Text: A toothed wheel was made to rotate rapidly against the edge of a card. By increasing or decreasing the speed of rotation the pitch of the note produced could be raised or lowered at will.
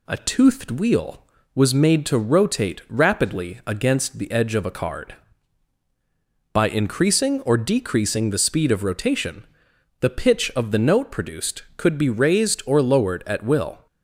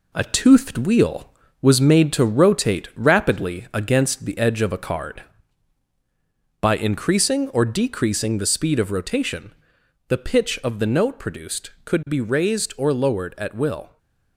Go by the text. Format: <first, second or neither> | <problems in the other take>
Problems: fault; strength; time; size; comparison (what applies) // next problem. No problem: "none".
first | gets quieter; noticeable; throughout; 5 dB // pauses between "rotation" and "the"; noticeable; at 9.5 s; 0.54 s long; noticeable in the first // stays silent after the last word; slight; from 13.8 s on; 0.5 s long